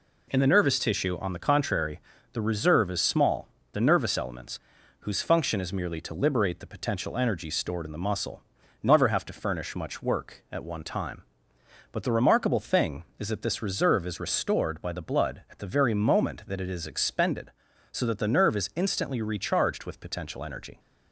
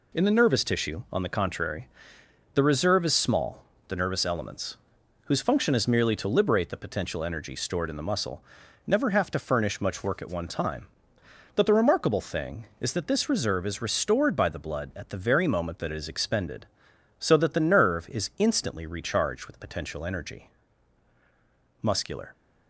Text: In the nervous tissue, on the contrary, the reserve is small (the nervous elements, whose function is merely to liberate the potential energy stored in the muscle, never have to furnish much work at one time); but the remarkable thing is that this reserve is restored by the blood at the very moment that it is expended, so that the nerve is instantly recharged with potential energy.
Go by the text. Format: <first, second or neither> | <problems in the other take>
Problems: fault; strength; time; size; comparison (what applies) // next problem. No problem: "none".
first | goes on to say "Muscular"; from 21.8 s on; 0.50 s long